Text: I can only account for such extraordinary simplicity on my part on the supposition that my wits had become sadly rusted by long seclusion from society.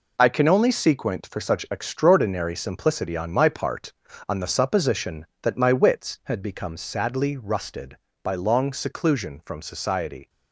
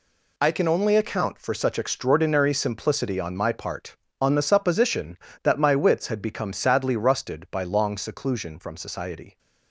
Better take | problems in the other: second | says "sequent" for "account"; at 0.6 s

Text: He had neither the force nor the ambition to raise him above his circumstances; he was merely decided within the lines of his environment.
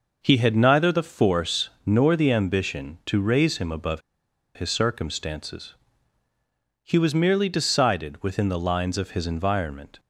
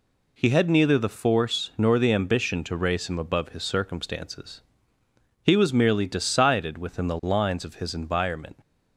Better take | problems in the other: second | pauses between "above" and "his"; noticeable; at 4.0 s; 0.54 s long

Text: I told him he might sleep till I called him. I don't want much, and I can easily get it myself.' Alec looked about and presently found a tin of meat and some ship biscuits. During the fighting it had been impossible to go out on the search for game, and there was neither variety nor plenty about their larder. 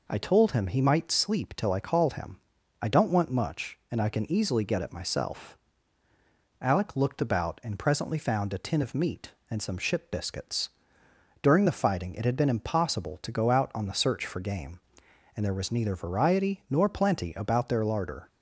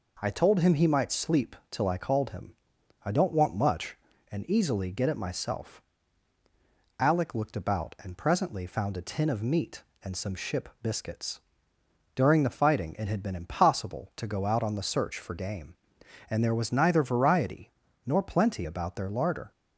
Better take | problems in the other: first | pauses between "sleep" and "till"; slight; at 1.5 s; 0.16 s long // skips "I can"; at 4.4 s // pauses between "variety" and "nor"; slight; at 17.6 s; 0.36 s long

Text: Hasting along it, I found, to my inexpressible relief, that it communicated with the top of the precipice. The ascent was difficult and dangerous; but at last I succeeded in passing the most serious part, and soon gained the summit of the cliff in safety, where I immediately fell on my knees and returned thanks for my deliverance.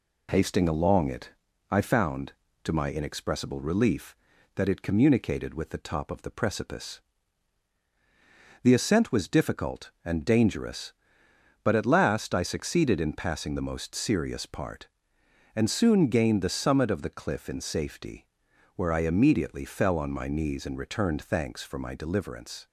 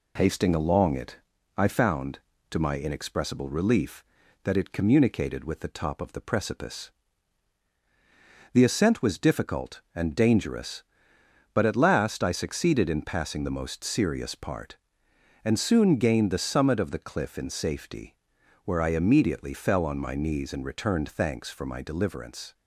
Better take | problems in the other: neither | none

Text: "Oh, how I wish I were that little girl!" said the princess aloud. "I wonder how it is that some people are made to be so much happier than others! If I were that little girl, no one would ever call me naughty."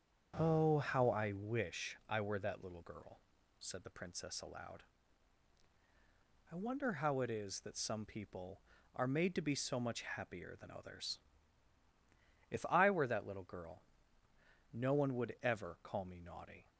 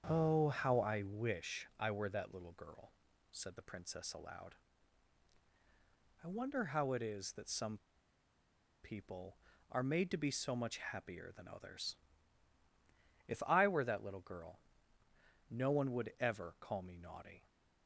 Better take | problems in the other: first | starts louder than the rest; strong; until 1.1 s; 7.5 dB; strong in the first // pauses between "some" and "people"; at 7.7 s; 1.0 s long

